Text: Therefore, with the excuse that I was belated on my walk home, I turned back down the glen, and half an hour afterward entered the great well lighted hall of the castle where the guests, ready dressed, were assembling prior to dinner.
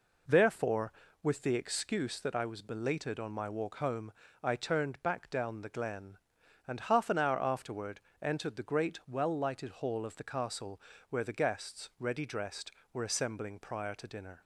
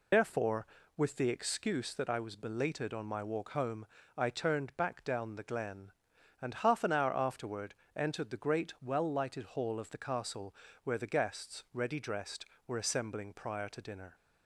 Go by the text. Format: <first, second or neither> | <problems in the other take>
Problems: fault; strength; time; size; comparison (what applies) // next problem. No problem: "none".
first | loses the start of "Therefore"; at 0.1 s; 110 ms // pauses between "afterward" and "entered"; slight; at 7.7 s; 0.20 s long; slight in the first // pauses between "castle" and "where"; slight; at 10.5 s; 0.30 s long; slight in the first